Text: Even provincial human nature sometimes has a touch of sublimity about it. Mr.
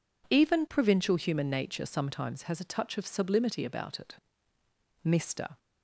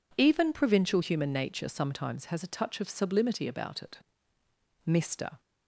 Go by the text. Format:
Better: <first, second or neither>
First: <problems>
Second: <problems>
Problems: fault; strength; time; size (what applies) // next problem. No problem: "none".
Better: neither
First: none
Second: none